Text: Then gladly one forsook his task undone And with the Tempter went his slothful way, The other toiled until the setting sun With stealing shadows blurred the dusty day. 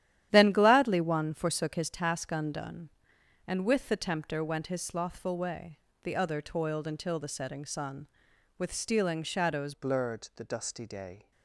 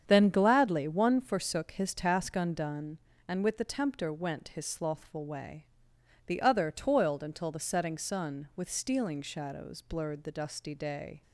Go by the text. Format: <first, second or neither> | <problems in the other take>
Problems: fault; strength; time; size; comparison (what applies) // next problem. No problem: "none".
second | starts louder than the rest; strong; until 1.3 s; 11.5 dB; strong in the second // changes voice at "blurred"; from 9.7 s on; 1.6 s long